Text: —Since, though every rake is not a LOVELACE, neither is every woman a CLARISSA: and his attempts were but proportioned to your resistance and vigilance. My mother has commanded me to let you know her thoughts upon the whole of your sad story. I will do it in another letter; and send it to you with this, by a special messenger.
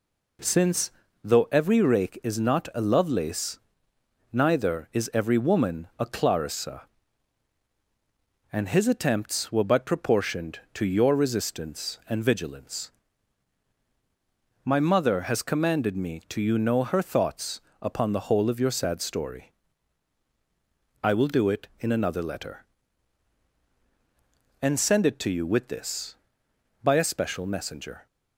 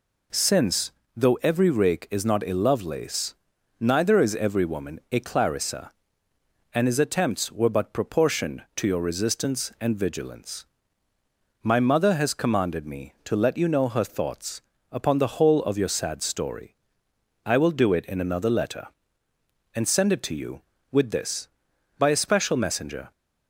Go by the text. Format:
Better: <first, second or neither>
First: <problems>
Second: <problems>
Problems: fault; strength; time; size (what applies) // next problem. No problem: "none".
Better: second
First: skips "let"; at 16.4 s // pauses between "thoughts" and "upon"; slight; at 17.6 s; 0.22 s long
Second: pauses between "thoughts" and "upon"; slight; at 14.6 s; 0.28 s long